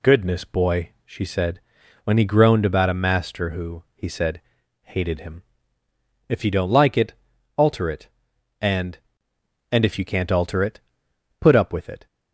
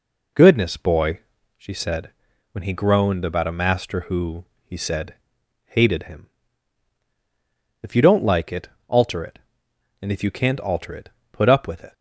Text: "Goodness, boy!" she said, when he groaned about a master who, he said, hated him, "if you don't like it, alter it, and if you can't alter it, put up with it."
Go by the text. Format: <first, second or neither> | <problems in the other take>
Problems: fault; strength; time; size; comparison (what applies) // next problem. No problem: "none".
second | says "and" twice; at 9.7 s